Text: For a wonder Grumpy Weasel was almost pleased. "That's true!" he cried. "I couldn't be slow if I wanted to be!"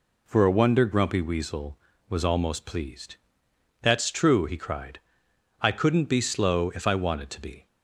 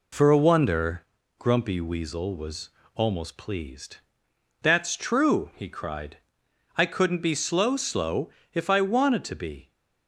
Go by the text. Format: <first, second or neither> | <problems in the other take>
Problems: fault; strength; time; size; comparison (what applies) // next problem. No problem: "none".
first | pauses between "wonder" and "Grumpy"; at 1.0 s; 0.38 s long // pauses between "was" and "almost"; slight; at 2.6 s; 0.24 s long // says "slow" twice; at 7.7 s